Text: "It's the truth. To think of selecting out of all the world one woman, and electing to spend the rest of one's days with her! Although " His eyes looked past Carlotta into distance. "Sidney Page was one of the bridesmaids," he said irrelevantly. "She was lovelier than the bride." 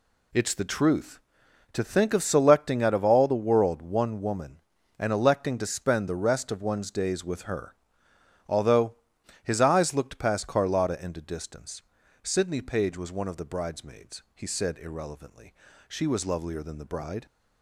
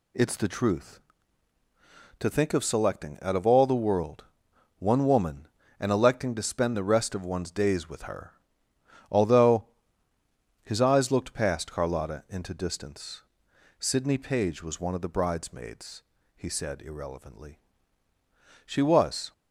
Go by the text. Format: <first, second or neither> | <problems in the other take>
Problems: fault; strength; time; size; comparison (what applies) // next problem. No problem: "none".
first | pauses between "world" and "one"; noticeable; at 4.2 s; 0.54 s long // stops before "lovelier than the bride"; at 19.3 s